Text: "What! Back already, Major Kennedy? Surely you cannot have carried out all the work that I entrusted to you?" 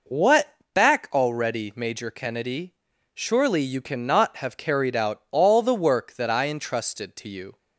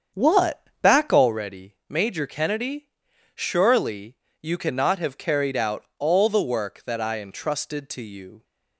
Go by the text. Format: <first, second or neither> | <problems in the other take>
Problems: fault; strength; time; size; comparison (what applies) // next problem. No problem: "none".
first | starts louder than the rest; strong; until 1.4 s; 7.5 dB // pauses between "Surely" and "you"; slight; at 4.1 s; 0.26 s long